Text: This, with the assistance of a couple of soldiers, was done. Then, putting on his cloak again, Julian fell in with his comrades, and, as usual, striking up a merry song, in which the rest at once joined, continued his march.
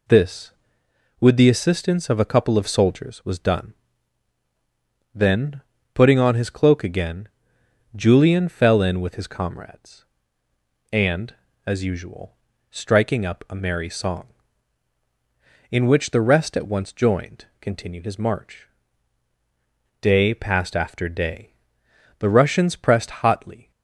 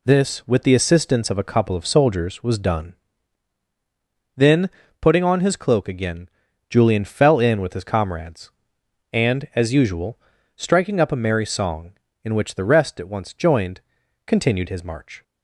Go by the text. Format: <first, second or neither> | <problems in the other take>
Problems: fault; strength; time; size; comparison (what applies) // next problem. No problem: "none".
second | goes on to say "Day passed after day The Russians pressed hotly"; strong; from 20.0 s on; 3.7 s long